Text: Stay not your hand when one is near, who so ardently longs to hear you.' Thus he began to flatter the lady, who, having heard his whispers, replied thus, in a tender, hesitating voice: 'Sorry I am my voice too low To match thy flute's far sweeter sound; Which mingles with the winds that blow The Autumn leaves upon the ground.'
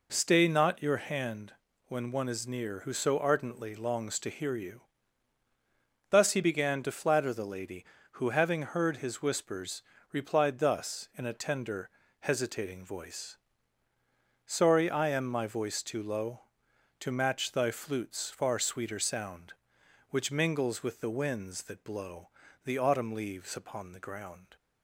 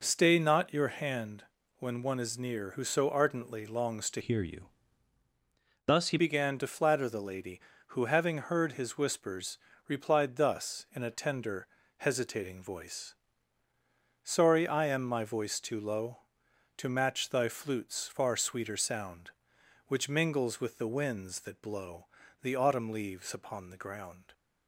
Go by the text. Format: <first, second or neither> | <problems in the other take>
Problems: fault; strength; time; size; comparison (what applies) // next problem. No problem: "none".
first | pauses between "hand" and "when"; slight; at 1.4 s; 0.34 s long; slight in the first // changes voice from "hear" to "he"; from 4.2 to 6.1 s; 1.9 s long // pauses between "blow" and "The"; slight; at 22.0 s; 0.34 s long; slight in the first